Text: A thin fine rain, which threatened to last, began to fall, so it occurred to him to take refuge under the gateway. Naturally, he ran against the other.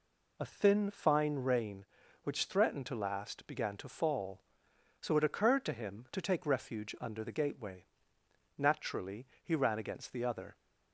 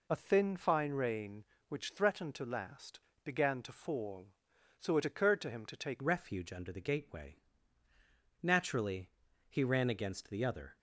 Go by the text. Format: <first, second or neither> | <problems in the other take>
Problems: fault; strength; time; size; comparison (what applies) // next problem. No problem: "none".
first | changes voice at "refuge"; from 6.0 s on; 4.7 s long